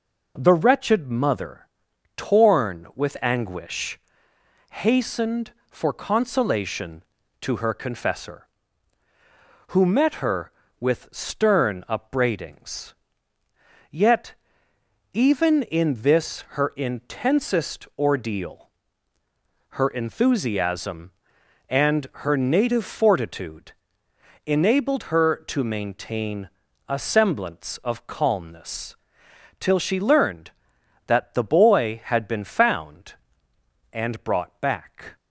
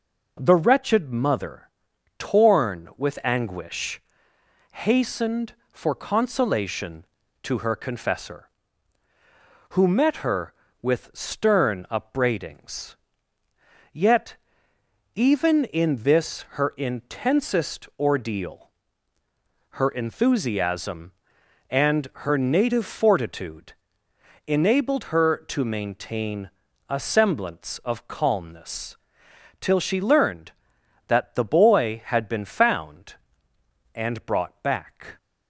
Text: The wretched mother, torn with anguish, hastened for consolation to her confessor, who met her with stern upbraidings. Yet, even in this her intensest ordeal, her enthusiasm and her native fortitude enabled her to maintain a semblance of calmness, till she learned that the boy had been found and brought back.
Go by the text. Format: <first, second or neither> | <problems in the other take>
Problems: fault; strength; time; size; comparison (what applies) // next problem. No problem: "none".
neither | pauses between "fortitude" and "enabled"; noticeable; the same in both // pauses between "maintain" and "a"; slight; the same in both